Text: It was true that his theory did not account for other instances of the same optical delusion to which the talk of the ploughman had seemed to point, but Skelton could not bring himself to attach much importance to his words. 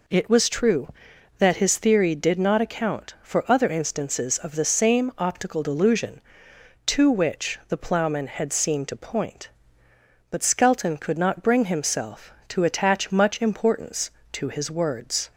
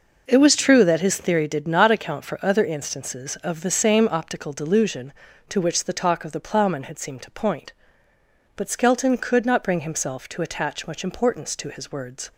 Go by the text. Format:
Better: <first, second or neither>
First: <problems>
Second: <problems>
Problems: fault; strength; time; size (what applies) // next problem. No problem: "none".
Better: second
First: skips "the talk of"; at 7.6 s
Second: none